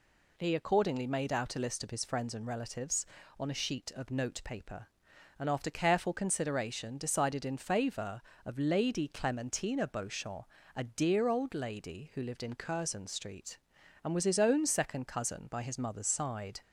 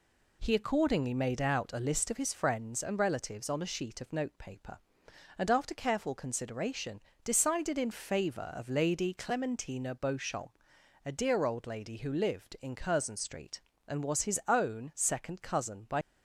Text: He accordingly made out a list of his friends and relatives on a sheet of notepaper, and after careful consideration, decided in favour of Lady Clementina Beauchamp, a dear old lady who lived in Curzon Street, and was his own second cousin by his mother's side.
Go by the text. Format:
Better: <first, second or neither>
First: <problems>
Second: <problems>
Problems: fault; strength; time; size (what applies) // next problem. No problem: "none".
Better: first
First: none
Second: stops before "his mother's side"; at 16.0 s